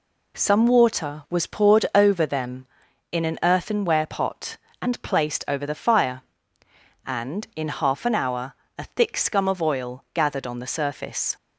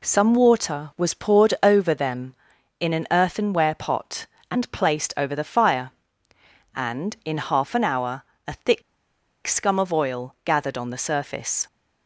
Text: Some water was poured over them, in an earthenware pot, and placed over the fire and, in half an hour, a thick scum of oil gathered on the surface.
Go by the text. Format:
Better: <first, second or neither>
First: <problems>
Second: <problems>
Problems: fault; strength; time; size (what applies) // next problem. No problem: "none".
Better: first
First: none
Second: pauses between "thick" and "scum"; noticeable; at 8.8 s; 0.64 s long